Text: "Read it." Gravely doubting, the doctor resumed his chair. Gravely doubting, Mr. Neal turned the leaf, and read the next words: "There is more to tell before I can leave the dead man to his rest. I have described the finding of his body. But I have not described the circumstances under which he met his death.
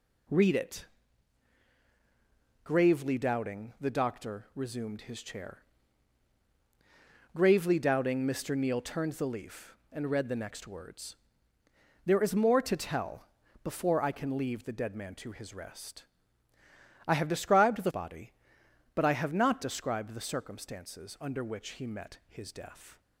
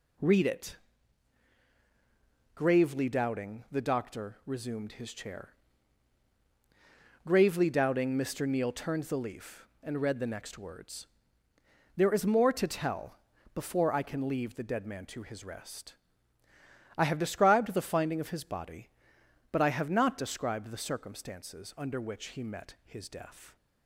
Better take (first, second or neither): second